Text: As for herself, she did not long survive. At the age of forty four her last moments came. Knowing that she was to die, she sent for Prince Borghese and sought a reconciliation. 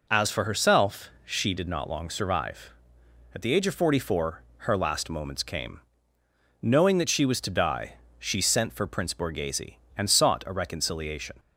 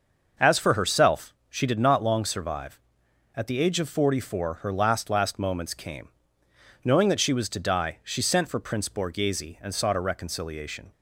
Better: first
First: none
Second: starts louder than the rest; noticeable; until 1.5 s; 6 dB // says "last" twice; at 5.0 s

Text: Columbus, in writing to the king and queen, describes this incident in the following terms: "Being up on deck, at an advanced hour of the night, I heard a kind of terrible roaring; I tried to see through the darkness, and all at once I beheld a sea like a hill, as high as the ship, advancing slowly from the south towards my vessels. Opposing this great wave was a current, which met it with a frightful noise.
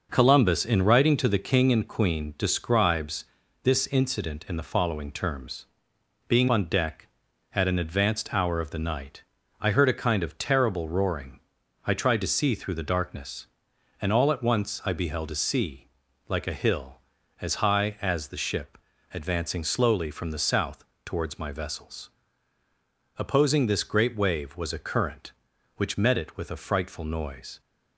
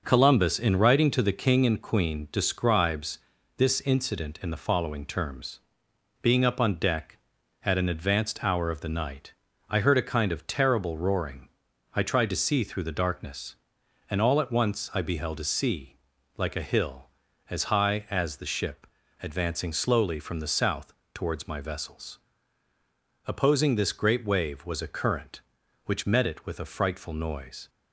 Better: second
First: pauses between "describes" and "this"; slight; at 3.2 s; 0.36 s long // skips "up"; at 6.4 s // pauses between "sea" and "like"; at 15.8 s; 0.40 s long // pauses between "south" and "towards"; slight; at 20.8 s; 0.20 s long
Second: pauses between "describes" and "this"; slight; at 3.2 s; 0.36 s long // pauses between "sea" and "like"; at 15.9 s; 0.40 s long // pauses between "south" and "towards"; slight; at 20.9 s; 0.20 s long

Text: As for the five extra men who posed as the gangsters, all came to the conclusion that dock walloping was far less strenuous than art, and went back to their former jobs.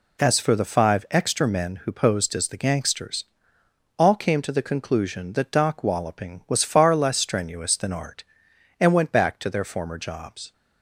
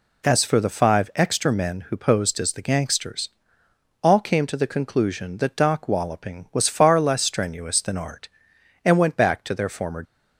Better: first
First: none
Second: stops before "jobs"; at 10.0 s

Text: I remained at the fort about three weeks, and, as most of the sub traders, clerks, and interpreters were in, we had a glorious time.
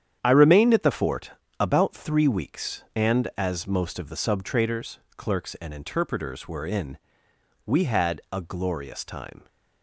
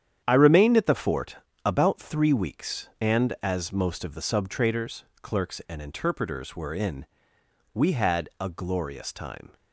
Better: neither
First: starts louder than the rest; strong; until 1.2 s; 9 dB // pauses between "fort" and "about"; slight; at 1.3 s; 0.28 s long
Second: starts louder than the rest; strong; until 1.2 s; 9 dB // pauses between "fort" and "about"; slight; at 1.3 s; 0.28 s long

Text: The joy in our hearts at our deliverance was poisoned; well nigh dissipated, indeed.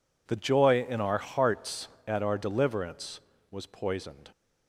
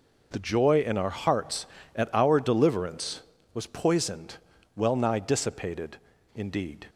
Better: second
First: stops before "well nigh dissipated indeed"; at 4.3 s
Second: none

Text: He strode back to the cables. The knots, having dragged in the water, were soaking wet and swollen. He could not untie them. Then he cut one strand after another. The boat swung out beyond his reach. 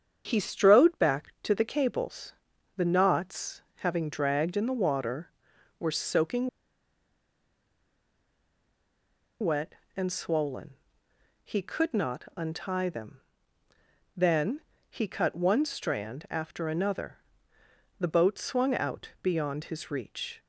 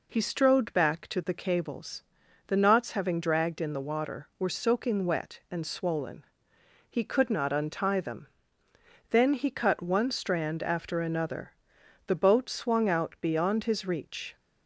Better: second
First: starts louder than the rest; strong; until 1.2 s; 7.5 dB // pauses between "soaking" and "wet"; strong; at 6.4 s; 2.9 s long // pauses between "Then" and "he"; slight; at 14.5 s; 0.28 s long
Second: none

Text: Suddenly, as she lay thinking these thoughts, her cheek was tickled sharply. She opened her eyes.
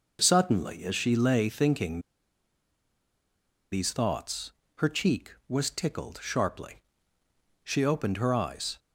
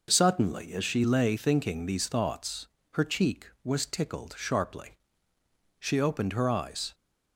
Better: second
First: pauses between "thinking" and "these"; strong; at 2.0 s; 1.7 s long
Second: none

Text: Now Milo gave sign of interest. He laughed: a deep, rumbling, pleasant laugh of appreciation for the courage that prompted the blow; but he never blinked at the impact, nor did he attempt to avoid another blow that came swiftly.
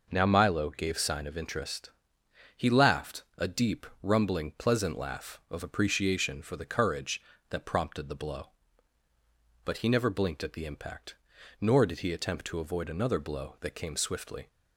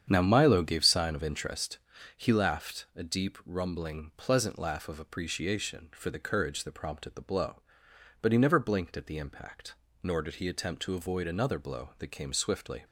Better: first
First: none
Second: starts louder than the rest; strong; until 1.5 s; 8.5 dB

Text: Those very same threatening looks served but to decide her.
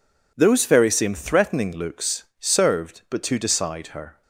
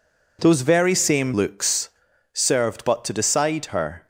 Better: first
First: pauses between "looks" and "served"; slight; at 2.2 s; 0.16 s long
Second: skips "threatening"; at 1.3 s // pauses between "looks" and "served"; at 1.8 s; 0.44 s long

